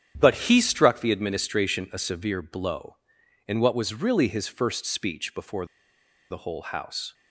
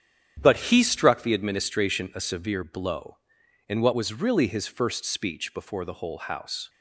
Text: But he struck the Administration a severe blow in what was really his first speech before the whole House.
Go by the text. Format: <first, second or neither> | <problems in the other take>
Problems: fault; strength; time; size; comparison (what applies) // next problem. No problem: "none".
second | starts louder than the rest; strong; until 1.1 s; 9.5 dB; strong in the second // pauses between "before" and "the"; noticeable; at 5.6 s; 0.64 s long